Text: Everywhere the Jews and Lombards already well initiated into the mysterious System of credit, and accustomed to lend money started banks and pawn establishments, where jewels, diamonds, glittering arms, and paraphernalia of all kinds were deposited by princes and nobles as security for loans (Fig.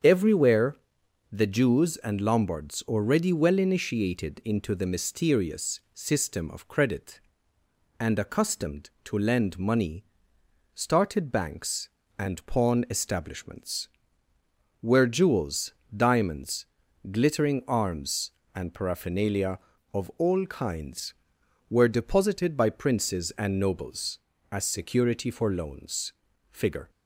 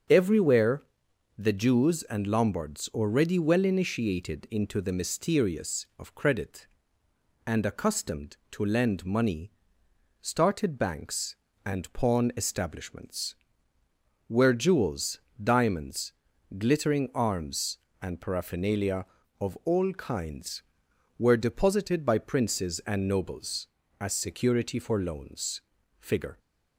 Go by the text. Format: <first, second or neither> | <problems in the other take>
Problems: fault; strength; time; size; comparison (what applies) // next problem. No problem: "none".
first | starts louder than the rest; until 1.6 s; 6.5 dB; strong in the first // pauses between "Everywhere" and "the"; noticeable; at 0.8 s; 0.56 s long; noticeable in the first // skips "System"; at 5.9 s // pauses between "money" and "started"; noticeable; at 9.5 s; 0.72 s long; noticeable in the first